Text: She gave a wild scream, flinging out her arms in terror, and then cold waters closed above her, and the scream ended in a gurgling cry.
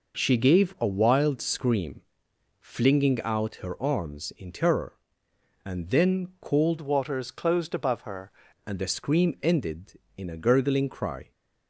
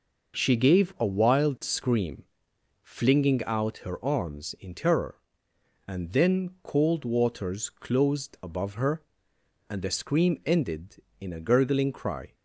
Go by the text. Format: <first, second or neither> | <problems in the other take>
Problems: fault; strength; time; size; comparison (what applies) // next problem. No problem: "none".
second | changes voice from "waters" to "her"; from 6.8 to 8.2 s; 1.4 s long